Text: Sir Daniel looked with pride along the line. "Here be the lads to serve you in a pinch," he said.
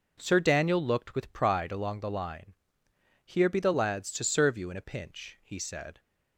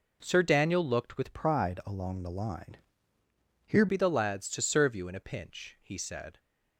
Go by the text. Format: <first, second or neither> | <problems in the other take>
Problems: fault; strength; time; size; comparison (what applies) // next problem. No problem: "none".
first | changes voice from "pride" to "Here"; from 1.3 to 3.8 s; 2.5 s long